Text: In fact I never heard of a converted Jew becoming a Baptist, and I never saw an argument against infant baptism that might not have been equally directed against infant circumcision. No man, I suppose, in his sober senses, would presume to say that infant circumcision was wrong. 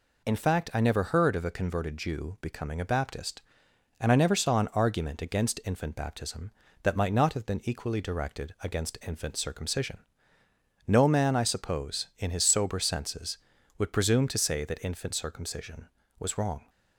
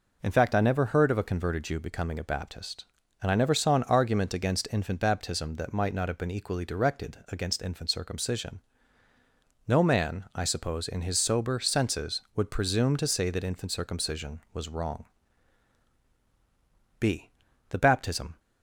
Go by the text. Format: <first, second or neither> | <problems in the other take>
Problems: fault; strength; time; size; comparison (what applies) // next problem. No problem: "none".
first | goes on to say "b The baptism"; from 16.9 s on; 1.4 s long